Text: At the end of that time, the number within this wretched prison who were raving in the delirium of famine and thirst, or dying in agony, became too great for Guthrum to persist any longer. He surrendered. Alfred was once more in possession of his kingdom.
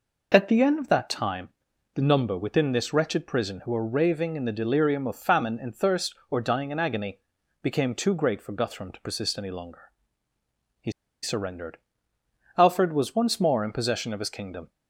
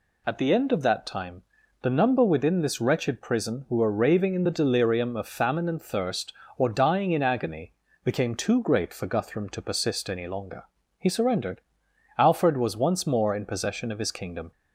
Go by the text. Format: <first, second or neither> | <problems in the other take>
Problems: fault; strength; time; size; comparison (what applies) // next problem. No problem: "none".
second | pauses between "He" and "surrendered"; slight; at 10.9 s; 0.31 s long